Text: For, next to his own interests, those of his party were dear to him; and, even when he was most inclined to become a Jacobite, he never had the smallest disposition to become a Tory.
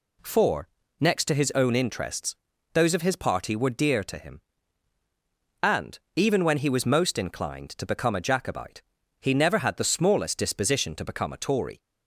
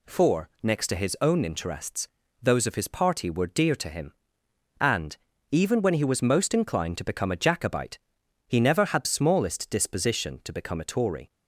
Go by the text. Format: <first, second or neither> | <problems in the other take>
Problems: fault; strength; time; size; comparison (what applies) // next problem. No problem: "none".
first | skips "the"; at 9.0 s